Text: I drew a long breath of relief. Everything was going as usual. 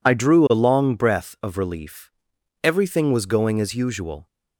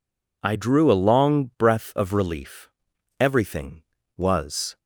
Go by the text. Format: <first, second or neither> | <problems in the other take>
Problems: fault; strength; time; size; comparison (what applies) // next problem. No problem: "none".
first | stops before "going as usual"; at 4.7 s